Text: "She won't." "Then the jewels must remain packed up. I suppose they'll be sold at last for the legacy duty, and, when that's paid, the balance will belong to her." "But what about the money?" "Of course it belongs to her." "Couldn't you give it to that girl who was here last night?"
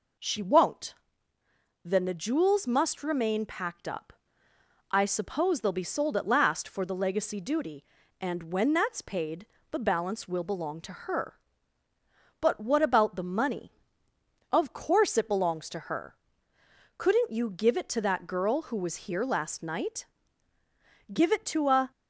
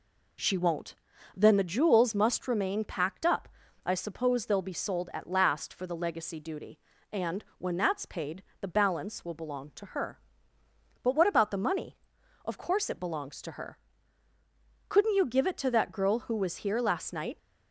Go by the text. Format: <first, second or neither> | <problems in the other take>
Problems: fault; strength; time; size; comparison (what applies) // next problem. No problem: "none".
second | goes on to say "Give it to a"; noticeable; from 21.0 s on; 0.84 s long